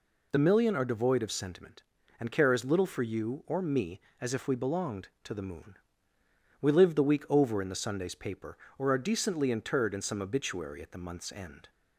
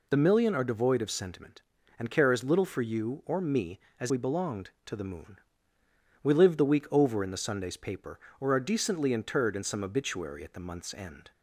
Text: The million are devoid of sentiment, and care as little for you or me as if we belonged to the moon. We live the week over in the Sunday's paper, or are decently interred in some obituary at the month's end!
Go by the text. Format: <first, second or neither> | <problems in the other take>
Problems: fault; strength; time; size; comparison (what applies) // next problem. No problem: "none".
first | skips "if"; at 4.0 s